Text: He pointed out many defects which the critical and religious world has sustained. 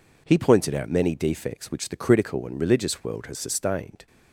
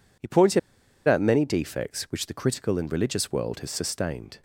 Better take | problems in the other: first | pauses between "pointed" and "out"; noticeable; at 0.5 s; 0.48 s long

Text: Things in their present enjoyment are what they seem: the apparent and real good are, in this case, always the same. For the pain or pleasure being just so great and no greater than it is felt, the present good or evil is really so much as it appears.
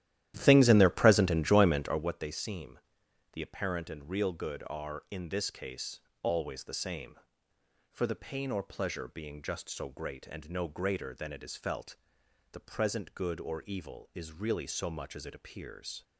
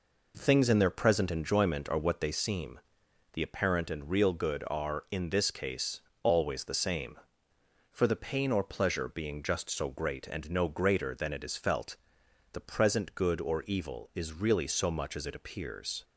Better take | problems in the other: second | starts louder than the rest; strong; until 2.1 s; 12.5 dB

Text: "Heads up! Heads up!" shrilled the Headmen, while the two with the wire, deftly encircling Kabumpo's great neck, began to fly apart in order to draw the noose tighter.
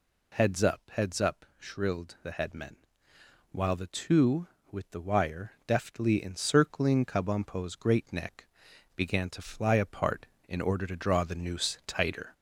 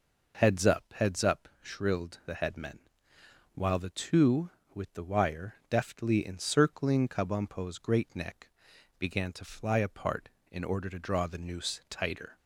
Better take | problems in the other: second | gets louder; throughout; 3.5 dB

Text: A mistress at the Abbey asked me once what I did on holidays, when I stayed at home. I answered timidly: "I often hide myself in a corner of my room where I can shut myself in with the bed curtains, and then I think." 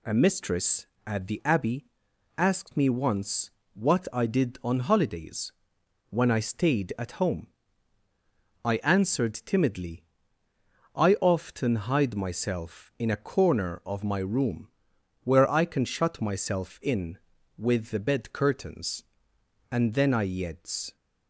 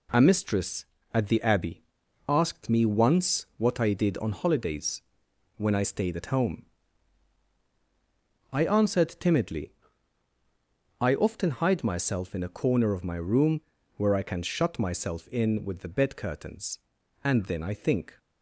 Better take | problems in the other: second | pauses between "Abbey" and "asked"; noticeable; at 1.8 s; 0.52 s long; also in the second // pauses between "once" and "what"; slight; at 3.5 s; 0.24 s long // pauses between "room" and "where"; noticeable; at 14.6 s; 0.54 s long; also in the second // says "yeds" for "think"; at 20.2 s

